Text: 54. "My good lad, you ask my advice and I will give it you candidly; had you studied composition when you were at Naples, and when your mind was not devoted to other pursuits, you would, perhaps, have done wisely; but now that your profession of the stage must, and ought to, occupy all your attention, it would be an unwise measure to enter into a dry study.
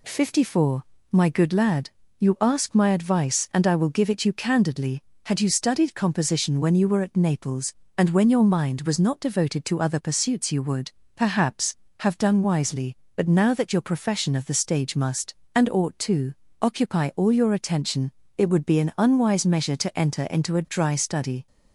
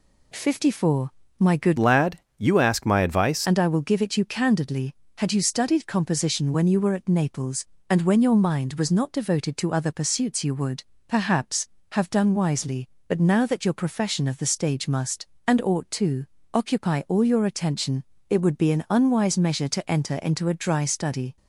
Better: first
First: none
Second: changes voice from "lad" to "advice"; from 1.7 to 3.4 s; 1.7 s long

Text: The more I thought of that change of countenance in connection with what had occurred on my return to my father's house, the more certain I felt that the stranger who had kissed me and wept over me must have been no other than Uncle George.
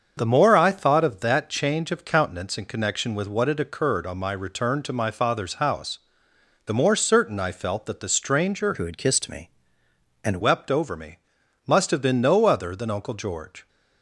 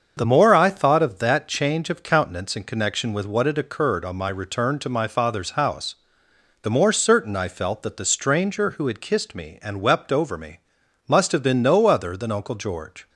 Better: second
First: starts louder than the rest; until 1.1 s; 7 dB // changes voice from "who" to "and"; from 8.7 to 10.4 s; 1.7 s long // pauses between "me" and "must"; noticeable; at 11.1 s; 0.48 s long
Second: starts louder than the rest; until 1.1 s; 7 dB // pauses between "me" and "must"; noticeable; at 10.6 s; 0.48 s long

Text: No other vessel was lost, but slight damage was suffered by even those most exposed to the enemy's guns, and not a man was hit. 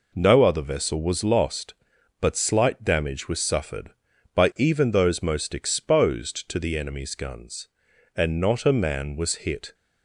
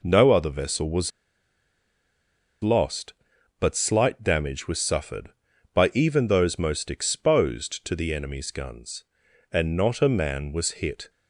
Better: first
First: none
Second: pauses between "was" and "lost"; strong; at 1.1 s; 1.5 s long

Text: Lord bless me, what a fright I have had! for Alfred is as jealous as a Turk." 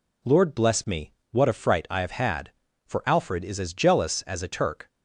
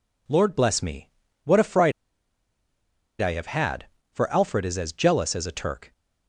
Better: first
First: none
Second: pauses between "fright" and "I"; strong; at 1.9 s; 1.2 s long

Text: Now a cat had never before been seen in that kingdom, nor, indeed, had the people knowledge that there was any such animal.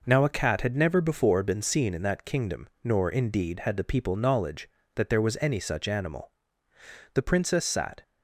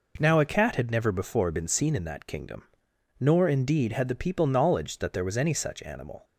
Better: second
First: goes on to say "The princess sat"; noticeable; from 7.1 s on; 0.88 s long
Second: none

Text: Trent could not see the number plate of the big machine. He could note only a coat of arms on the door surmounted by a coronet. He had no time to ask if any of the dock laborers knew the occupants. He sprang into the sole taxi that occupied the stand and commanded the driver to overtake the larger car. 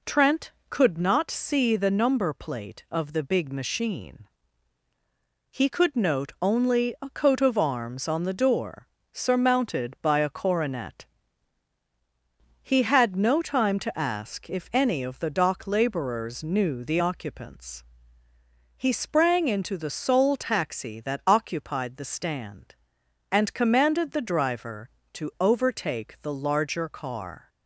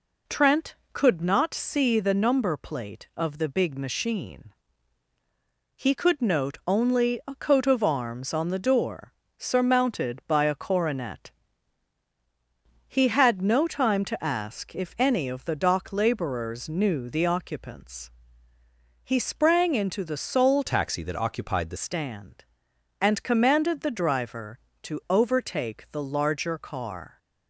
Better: first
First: pauses between "door" and "surmounted"; slight; at 8.8 s; 0.26 s long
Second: pauses between "door" and "surmounted"; slight; at 9.1 s; 0.26 s long // changes voice from "taxi" to "the"; from 20.6 to 21.7 s; 1.1 s long

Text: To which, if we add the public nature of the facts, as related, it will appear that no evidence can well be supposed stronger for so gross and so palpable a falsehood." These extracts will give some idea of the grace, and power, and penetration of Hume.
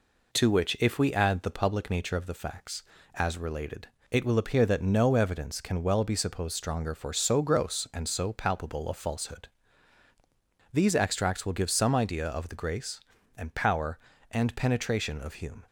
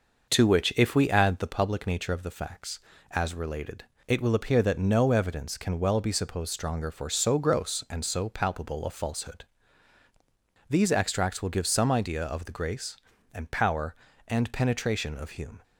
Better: first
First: none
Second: starts louder than the rest; noticeable; until 1.4 s; 6 dB

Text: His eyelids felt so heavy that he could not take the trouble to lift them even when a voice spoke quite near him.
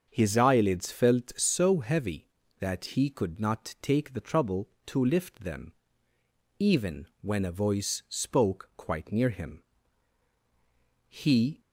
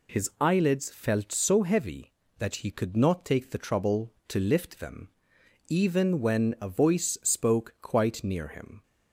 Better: second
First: starts louder than the rest; until 1.1 s; 6.5 dB // pauses between "them" and "even"; noticeable; at 5.7 s; 0.88 s long // pauses between "even" and "when"; slight; at 7.0 s; 0.16 s long // goes on to say "He"; from 11.0 s on; 0.52 s long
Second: pauses between "them" and "even"; noticeable; at 5.1 s; 0.58 s long

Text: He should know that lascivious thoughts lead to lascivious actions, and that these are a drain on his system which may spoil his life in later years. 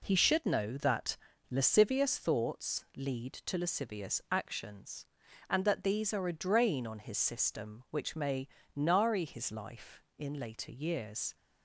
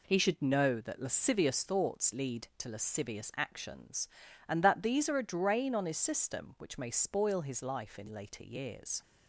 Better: second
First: pauses between "that" and "lascivious"; slight; at 1.1 s; 0.34 s long // says "nari" for "spoil"; at 8.7 s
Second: none

